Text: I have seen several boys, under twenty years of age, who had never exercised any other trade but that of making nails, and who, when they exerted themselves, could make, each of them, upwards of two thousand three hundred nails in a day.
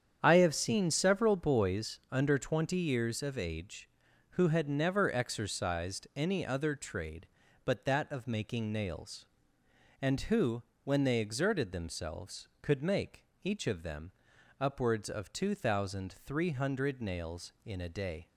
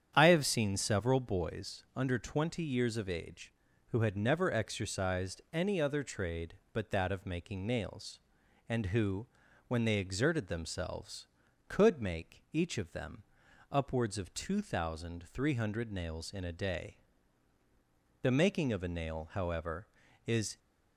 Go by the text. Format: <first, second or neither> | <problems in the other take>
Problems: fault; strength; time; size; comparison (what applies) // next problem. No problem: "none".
first | starts louder than the rest; strong; until 1.1 s; 9 dB; strong in the first // goes on to say "The making of a nail however is"; strong; from 18.2 s on; 2.3 s long